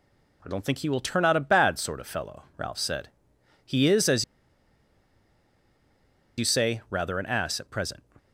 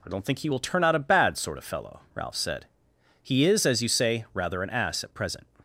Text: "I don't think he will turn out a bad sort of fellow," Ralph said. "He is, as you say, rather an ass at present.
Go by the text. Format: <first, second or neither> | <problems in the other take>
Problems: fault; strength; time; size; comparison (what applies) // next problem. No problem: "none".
second | pauses between "as" and "you"; strong; at 4.2 s; 2.1 s long